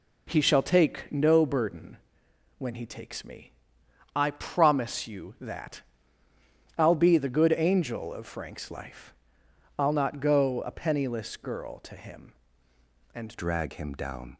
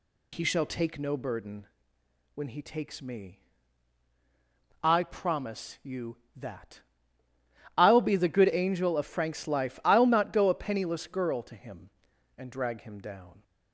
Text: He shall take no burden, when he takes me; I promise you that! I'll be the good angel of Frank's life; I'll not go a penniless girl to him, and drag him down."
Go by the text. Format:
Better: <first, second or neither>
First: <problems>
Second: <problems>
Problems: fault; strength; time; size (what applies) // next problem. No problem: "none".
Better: second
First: changes voice at "drag"; from 13.3 s on; 1.0 s long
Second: none